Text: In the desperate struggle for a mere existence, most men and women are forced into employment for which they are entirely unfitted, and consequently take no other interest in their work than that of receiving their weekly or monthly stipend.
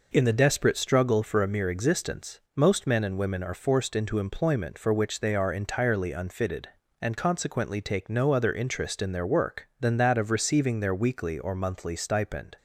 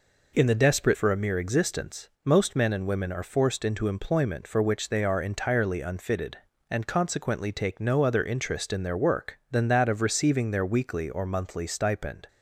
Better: first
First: none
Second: skips "struggle"; at 0.9 s

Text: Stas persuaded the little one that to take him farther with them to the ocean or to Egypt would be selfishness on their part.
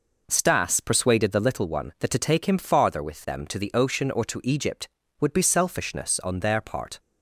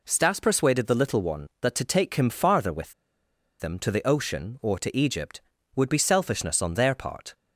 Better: first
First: none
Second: pauses between "with" and "them"; noticeable; at 2.9 s; 0.68 s long

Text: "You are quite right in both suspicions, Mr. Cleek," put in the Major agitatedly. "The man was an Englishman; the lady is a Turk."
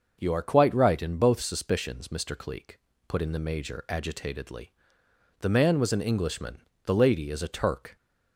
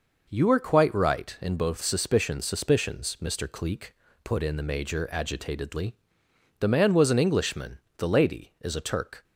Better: first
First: none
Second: says "suspicions" twice; at 2.4 s

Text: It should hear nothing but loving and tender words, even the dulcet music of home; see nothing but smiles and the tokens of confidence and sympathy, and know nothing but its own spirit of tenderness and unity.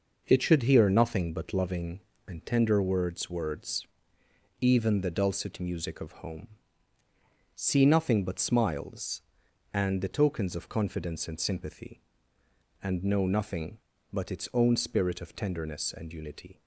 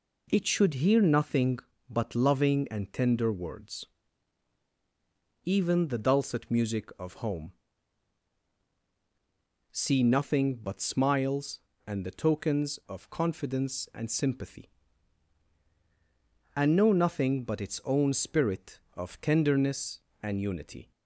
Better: second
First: says "words" twice; at 3.2 s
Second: none

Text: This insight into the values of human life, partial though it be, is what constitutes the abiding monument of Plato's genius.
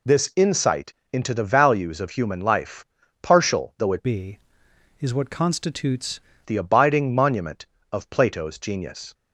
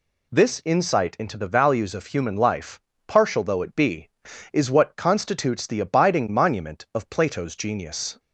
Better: second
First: pauses between "insight" and "into"; slight; at 0.9 s; 0.18 s long // changes voice from "be" to "constitutes"; from 4.0 to 6.2 s; 2.2 s long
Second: none

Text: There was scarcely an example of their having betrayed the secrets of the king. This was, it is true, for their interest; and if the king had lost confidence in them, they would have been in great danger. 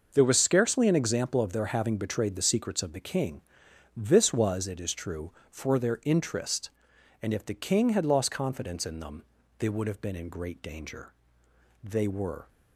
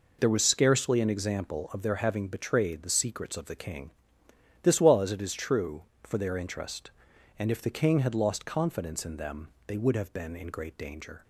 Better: second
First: goes on to say "They were"; noticeable; from 11.8 s on; 0.64 s long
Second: none

